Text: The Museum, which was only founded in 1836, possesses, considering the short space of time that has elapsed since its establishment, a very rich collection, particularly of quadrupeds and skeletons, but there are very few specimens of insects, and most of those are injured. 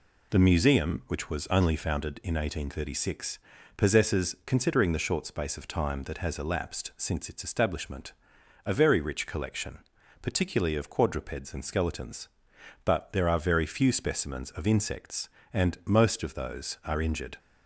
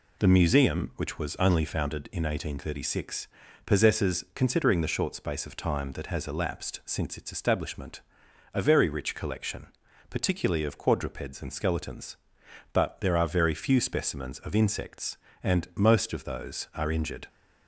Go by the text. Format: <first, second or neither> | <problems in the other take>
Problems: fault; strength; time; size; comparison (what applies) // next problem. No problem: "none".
neither | none